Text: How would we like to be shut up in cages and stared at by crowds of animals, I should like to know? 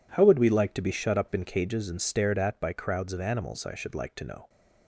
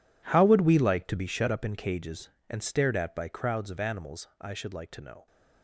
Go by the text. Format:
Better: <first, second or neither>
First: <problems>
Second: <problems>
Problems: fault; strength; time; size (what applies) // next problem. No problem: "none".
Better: first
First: none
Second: gets quieter; strong; throughout; 17 dB